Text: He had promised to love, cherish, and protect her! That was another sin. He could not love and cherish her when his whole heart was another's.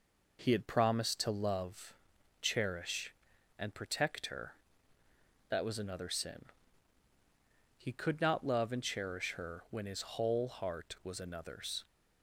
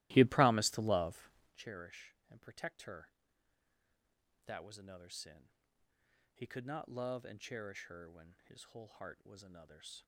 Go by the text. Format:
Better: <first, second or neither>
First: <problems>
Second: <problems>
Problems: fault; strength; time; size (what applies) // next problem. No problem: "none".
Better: first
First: none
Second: starts louder than the rest; strong; until 1.6 s; 17 dB